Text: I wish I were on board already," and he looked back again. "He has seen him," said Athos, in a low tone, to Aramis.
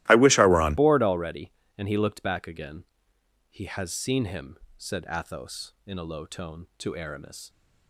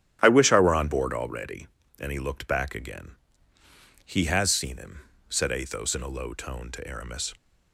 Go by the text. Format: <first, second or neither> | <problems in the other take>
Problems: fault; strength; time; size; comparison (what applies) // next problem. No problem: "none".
second | starts louder than the rest; strong; until 1.1 s; 16.5 dB; strong in the second // changes voice at "board"; from 0.7 s on; 6.7 s long